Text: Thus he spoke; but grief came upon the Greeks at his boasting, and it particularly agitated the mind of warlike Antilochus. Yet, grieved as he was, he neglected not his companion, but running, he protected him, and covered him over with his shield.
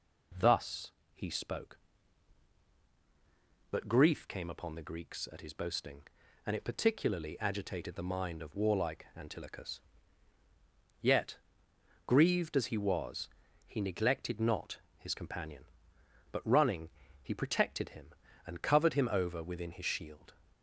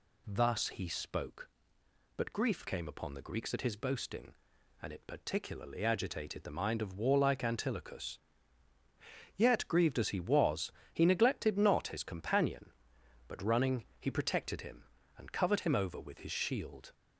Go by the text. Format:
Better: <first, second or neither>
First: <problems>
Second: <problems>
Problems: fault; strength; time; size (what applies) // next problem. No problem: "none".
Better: second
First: pauses between "Thus" and "he"; slight; at 0.9 s; 0.22 s long // pauses between "not" and "his"; slight; at 14.7 s; 0.18 s long // says "within" for "with"; at 19.4 s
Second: none